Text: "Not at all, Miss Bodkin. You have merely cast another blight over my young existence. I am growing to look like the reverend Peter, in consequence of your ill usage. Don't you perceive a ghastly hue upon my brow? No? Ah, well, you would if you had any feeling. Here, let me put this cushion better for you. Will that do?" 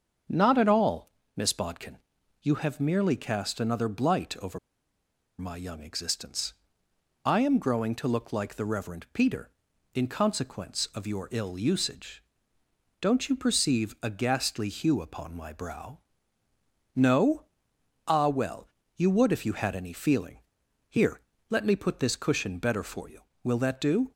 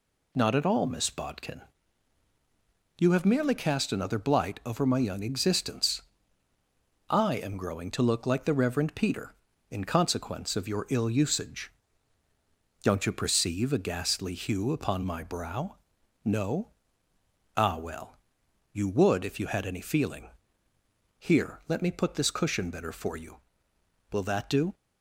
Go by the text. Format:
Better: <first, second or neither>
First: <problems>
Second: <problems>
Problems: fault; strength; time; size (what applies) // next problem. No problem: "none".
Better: second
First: starts louder than the rest; until 1.5 s; 6.5 dB // pauses between "over" and "my"; noticeable; at 4.5 s; 0.80 s long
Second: none